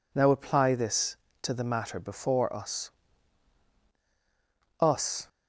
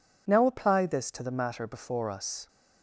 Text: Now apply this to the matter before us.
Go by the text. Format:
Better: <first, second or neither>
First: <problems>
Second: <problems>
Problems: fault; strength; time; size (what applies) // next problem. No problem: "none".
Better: second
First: says "us" twice; at 4.7 s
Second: none